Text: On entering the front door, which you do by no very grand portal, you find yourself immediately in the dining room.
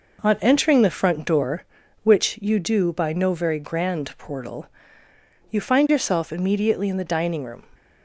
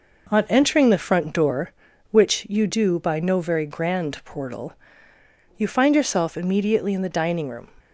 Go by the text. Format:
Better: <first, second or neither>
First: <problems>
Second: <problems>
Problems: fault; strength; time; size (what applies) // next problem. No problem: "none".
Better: neither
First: none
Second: none